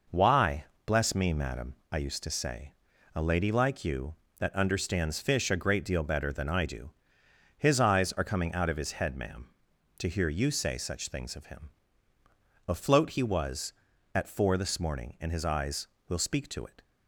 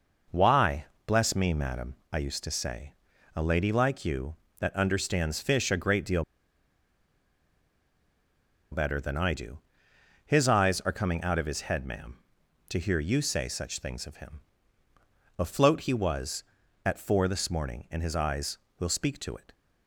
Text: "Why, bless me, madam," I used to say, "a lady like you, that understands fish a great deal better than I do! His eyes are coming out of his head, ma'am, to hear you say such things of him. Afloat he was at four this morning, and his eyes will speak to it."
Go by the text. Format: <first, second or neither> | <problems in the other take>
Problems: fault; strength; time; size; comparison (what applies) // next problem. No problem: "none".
first | pauses between "deal" and "better"; strong; at 6.2 s; 2.4 s long